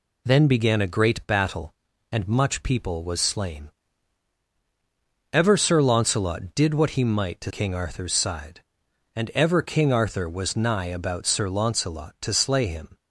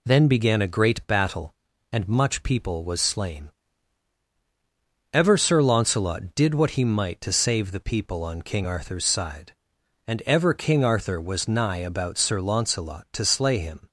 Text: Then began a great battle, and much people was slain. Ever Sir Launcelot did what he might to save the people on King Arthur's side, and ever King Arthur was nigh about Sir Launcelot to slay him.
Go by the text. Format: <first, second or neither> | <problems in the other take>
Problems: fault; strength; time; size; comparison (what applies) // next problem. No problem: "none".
second | skips "save the people on"; at 7.5 s